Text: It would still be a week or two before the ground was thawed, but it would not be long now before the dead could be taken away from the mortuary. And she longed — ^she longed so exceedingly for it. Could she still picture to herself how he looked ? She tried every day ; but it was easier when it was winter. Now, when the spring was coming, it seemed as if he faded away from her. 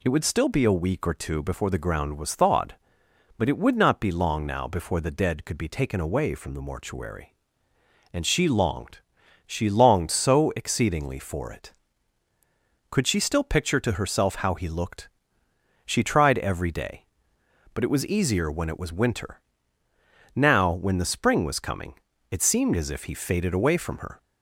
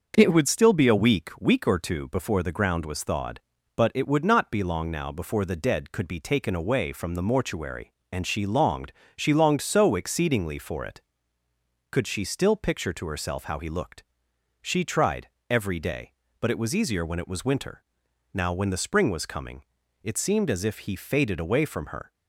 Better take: first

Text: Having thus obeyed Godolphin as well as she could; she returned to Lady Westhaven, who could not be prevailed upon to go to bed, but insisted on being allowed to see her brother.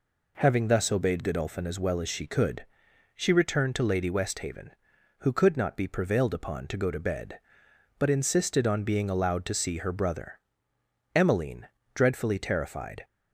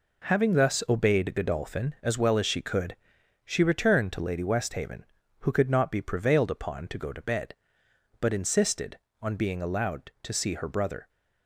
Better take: second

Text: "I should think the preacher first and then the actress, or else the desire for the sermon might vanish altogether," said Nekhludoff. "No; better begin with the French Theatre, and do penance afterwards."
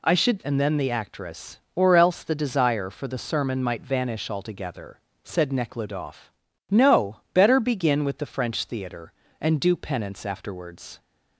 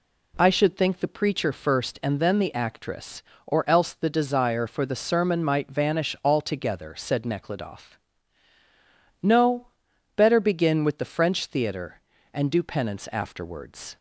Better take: second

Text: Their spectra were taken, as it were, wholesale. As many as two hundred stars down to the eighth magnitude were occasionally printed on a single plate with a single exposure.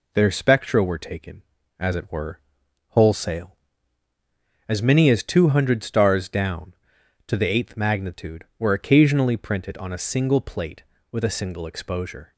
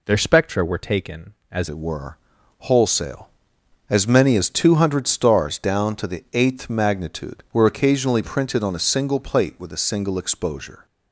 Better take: first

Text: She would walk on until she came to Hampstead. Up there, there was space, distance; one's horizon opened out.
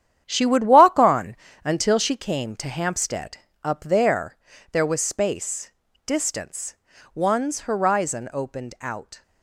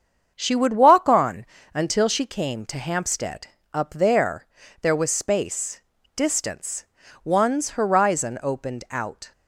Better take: second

